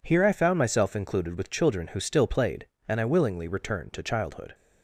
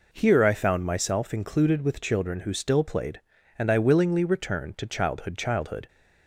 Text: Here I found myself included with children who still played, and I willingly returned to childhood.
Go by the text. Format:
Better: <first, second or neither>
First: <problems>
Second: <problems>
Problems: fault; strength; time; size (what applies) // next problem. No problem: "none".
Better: first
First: none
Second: says "childhood" twice; at 5.3 s